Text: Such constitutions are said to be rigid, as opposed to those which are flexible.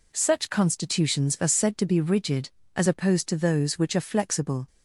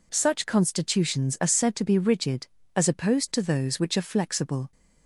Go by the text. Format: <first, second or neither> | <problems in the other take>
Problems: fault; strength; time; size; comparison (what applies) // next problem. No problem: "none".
neither | none